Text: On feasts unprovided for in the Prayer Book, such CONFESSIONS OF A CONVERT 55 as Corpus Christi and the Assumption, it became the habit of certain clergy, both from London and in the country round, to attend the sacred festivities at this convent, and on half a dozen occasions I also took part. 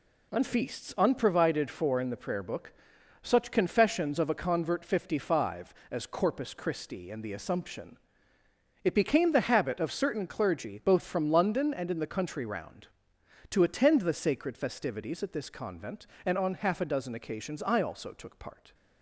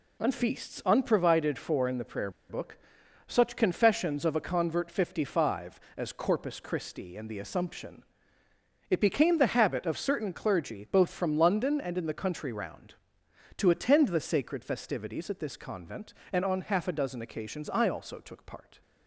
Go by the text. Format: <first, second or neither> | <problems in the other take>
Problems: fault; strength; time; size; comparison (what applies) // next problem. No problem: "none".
first | pauses between "Prayer" and "Book"; slight; at 2.2 s; 0.19 s long